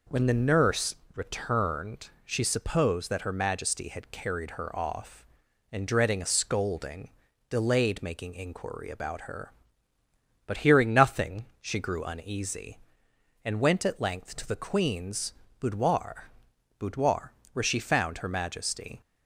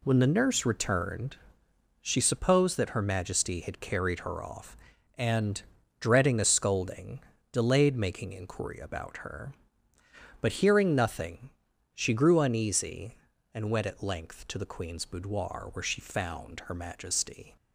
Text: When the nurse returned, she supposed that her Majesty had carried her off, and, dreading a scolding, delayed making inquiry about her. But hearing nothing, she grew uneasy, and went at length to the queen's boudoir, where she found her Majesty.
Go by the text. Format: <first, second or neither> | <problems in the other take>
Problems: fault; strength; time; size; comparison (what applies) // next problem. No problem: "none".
second | pauses between "nurse" and "returned"; slight; at 0.9 s; 0.20 s long // pauses between "queen's" and "boudoir"; slight; at 15.3 s; 0.26 s long // says "boudoir" twice; at 16.7 s